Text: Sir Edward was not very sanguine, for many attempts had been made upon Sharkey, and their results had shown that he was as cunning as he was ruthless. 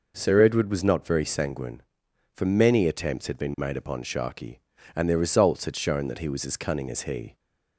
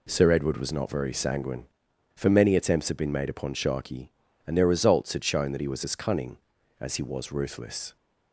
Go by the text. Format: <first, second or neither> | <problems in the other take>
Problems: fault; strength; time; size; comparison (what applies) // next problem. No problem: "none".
second | stops before "was ruthless"; at 7.3 s